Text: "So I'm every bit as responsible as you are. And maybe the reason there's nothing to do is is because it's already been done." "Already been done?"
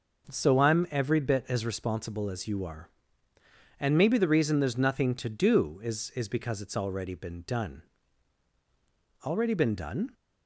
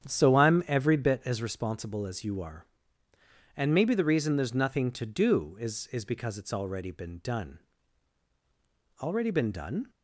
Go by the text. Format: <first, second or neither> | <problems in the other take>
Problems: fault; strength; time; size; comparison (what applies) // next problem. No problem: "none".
first | starts louder than the rest; strong; until 1.3 s; 9 dB